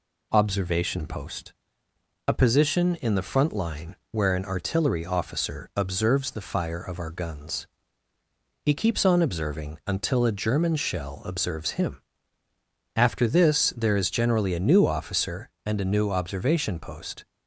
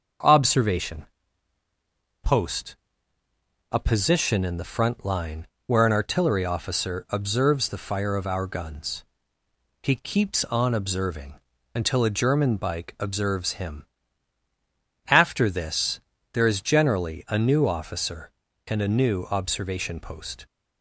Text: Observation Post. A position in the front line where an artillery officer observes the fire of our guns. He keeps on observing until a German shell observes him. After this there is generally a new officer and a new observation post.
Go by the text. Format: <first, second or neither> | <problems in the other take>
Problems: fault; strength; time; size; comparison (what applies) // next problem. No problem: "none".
first | starts louder than the rest; until 2.4 s; 6.5 dB // pauses between "Observation" and "Post"; at 1.0 s; 1.1 s long // pauses between "line" and "where"; slight; at 5.4 s; 0.18 s long; slight in the first // pauses between "observing" and "until"; slight; at 11.3 s; 0.34 s long // says "bike" for "shell"; at 12.5 s // pauses between "this" and "there"; slight; at 15.9 s; 0.34 s long